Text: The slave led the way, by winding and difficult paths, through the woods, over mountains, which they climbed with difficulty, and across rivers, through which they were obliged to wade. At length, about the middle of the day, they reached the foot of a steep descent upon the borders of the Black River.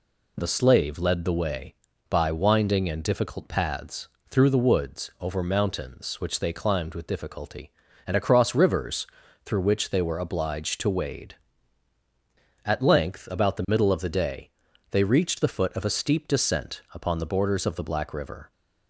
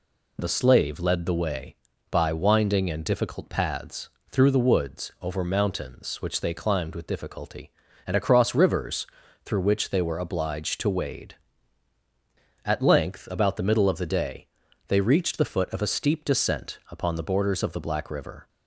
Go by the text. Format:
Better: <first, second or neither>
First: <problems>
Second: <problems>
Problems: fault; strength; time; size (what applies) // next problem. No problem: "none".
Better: neither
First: none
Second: none